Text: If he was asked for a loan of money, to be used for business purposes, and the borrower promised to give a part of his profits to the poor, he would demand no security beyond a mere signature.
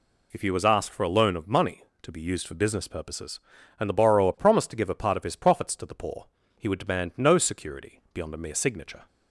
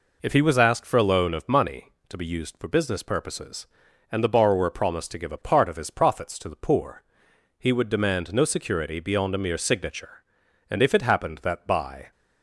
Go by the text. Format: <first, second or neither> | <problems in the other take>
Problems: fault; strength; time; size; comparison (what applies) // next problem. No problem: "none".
first | goes on to say "And if it happened that by"; from 10.6 s on; 1.4 s long